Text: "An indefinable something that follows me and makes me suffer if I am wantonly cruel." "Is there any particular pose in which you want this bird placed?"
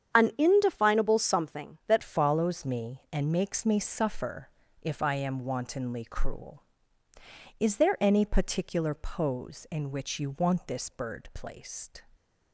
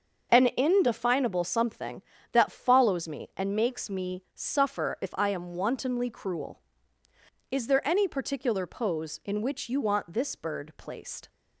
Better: second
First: starts louder than the rest; strong; until 1.2 s; 8.5 dB // changes voice at "follows"; from 2.0 s on; 10.0 s long // pauses between "suffer" and "if"; slight; at 4.4 s; 0.32 s long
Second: starts louder than the rest; until 1.4 s; 6.5 dB

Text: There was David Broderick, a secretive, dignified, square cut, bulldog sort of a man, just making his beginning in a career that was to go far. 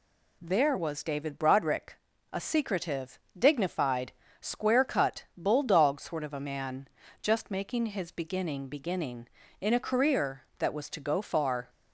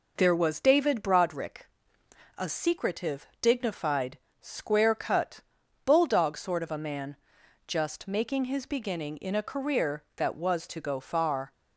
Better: second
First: says "beginning" twice; at 8.6 s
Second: none

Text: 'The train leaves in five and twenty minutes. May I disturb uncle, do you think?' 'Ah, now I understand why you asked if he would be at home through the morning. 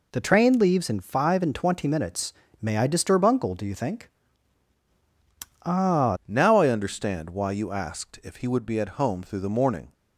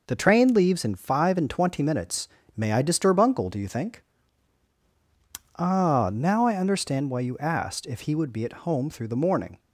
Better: second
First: changes voice at "now"; from 6.2 s on; 3.7 s long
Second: none

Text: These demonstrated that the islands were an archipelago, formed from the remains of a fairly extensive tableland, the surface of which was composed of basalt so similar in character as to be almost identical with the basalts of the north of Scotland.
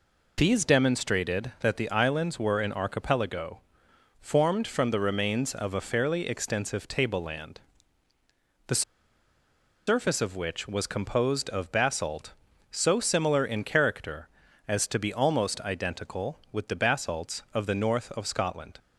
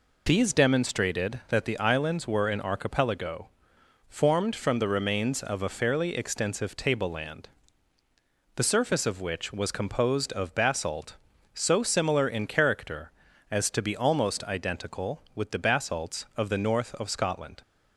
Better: second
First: pauses between "the" and "surface"; at 8.8 s; 1.0 s long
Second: none

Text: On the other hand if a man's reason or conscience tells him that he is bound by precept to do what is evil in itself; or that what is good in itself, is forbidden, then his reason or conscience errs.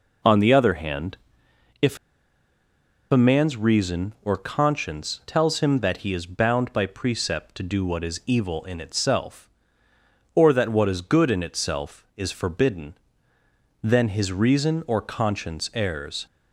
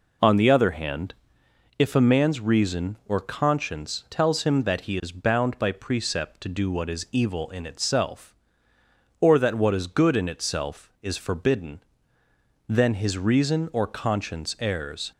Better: second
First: pauses between "hand" and "if"; noticeable; at 1.1 s; 0.64 s long // pauses between "if" and "a"; at 1.9 s; 1.1 s long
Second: pauses between "hand" and "if"; noticeable; at 1.1 s; 0.64 s long

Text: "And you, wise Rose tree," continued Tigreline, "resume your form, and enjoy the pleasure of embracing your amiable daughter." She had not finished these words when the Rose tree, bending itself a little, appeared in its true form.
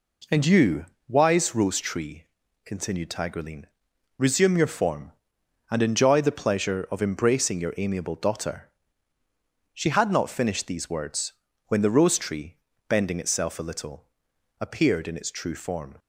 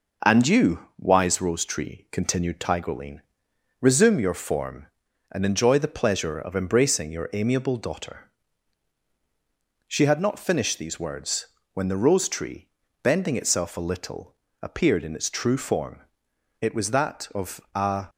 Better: first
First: pauses between "words" and "when"; slight; at 11.3 s; 0.34 s long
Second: pauses between "words" and "when"; slight; at 11.4 s; 0.26 s long // goes on to say "It was that of a"; from 16.6 s on; 1.4 s long

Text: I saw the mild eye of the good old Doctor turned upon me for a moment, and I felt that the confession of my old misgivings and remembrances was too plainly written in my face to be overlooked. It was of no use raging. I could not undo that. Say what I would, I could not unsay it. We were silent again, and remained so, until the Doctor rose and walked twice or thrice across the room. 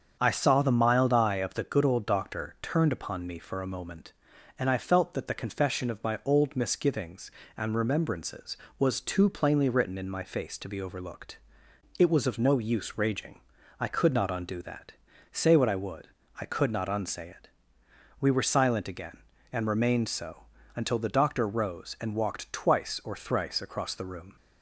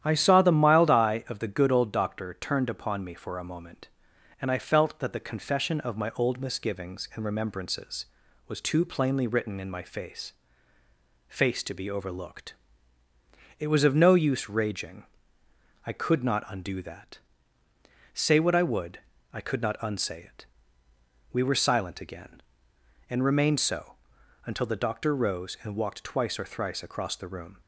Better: first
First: starts louder than the rest; until 1.2 s; 7 dB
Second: starts louder than the rest; strong; until 1.0 s; 10.5 dB // says "face" twice; at 11.2 s

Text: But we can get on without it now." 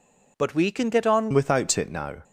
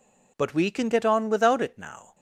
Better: second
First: changes voice at "without"; from 1.3 s on; 0.9 s long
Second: none

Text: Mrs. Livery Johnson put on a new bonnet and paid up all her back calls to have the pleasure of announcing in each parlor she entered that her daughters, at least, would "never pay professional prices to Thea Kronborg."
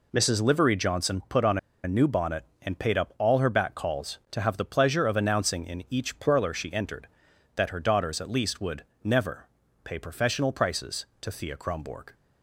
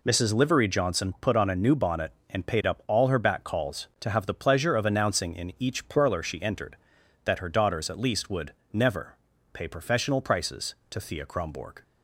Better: second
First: pauses between "on" and "a"; slight; at 1.5 s; 0.26 s long // pauses between "would" and "never"; slight; at 8.8 s; 0.20 s long // pauses between "never" and "pay"; slight; at 9.4 s; 0.36 s long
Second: pauses between "would" and "never"; slight; at 8.5 s; 0.20 s long // pauses between "never" and "pay"; slight; at 9.1 s; 0.36 s long

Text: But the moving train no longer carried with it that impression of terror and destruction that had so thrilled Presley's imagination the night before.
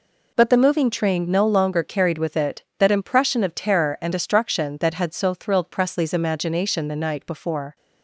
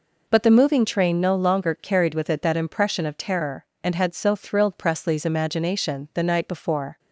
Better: first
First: none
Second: skips "destruction that"; at 3.9 s

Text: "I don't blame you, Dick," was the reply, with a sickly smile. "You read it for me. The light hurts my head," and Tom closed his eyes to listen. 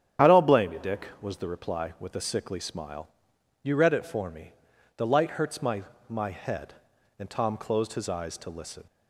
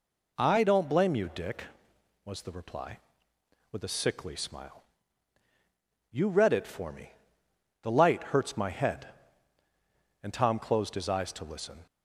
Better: second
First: starts louder than the rest; strong; until 1.3 s; 9.5 dB // says "my" twice; at 6.1 s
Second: none

